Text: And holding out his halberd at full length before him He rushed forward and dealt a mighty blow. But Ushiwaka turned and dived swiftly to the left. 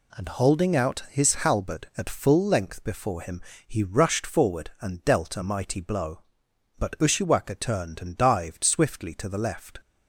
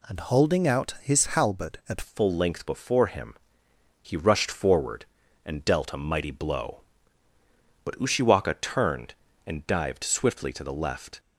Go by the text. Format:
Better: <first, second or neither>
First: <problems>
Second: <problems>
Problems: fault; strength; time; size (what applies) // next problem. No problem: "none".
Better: first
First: pauses between "him" and "He"; slight; at 3.4 s; 0.24 s long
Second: changes voice at "full"; from 2.0 s on; 9.1 s long // pauses between "him" and "He"; noticeable; at 3.3 s; 0.68 s long